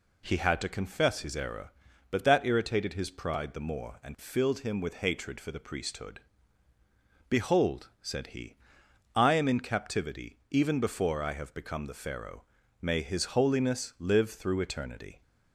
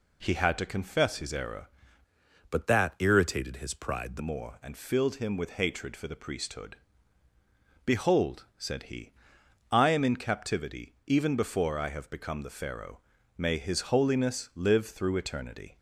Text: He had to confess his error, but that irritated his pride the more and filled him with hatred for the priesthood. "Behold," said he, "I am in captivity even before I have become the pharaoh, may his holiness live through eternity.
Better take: first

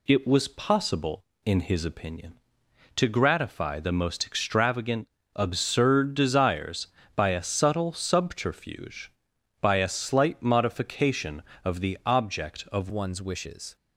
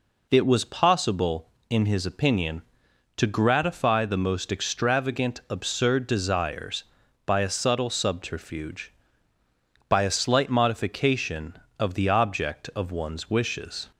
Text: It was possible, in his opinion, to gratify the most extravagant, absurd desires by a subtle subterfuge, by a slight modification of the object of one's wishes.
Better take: second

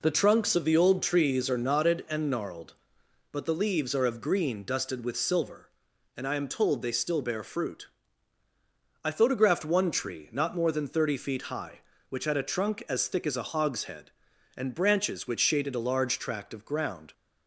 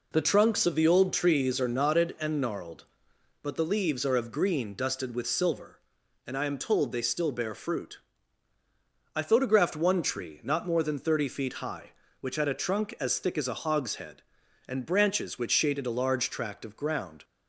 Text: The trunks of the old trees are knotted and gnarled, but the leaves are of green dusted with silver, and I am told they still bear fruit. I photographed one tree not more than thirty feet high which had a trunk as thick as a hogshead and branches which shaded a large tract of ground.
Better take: neither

